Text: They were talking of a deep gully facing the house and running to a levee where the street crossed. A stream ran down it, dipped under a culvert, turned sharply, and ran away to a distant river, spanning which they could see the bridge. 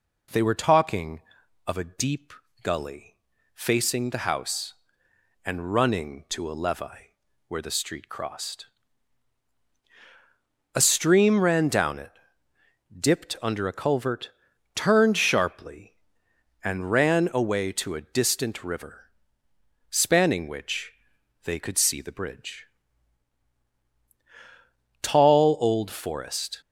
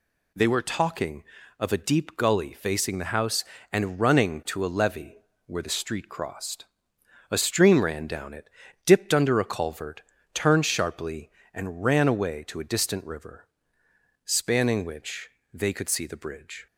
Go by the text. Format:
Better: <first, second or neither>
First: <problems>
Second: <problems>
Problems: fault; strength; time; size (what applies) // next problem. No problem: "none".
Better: second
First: pauses between "deep" and "gully"; slight; at 2.3 s; 0.28 s long // pauses between "gully" and "facing"; at 3.1 s; 0.40 s long // pauses between "levee" and "where"; slight; at 7.1 s; 0.32 s long // pauses between "which" and "they"; noticeable; at 20.9 s; 0.52 s long // goes on to say "Tall old forest"; from 25.0 s on; 1.6 s long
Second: pauses between "levee" and "where"; slight; at 5.1 s; 0.28 s long // pauses between "which" and "they"; slight; at 15.2 s; 0.24 s long